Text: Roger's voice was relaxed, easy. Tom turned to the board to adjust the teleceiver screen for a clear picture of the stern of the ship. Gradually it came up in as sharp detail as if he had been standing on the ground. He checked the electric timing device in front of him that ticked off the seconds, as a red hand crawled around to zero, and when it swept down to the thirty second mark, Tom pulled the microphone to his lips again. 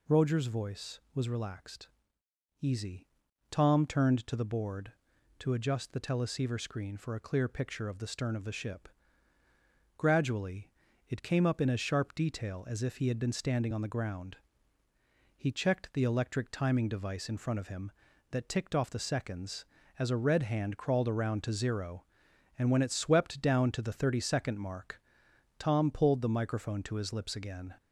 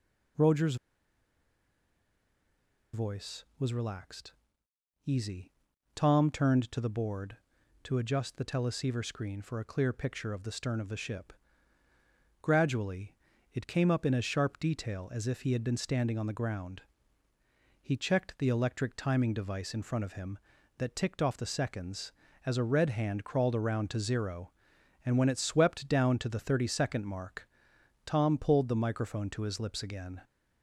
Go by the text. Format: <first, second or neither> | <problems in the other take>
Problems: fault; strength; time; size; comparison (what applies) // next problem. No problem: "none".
first | pauses between "Roger's" and "voice"; strong; at 0.7 s; 2.1 s long // pauses between "Gradually" and "it"; at 13.1 s; 0.38 s long; also in the first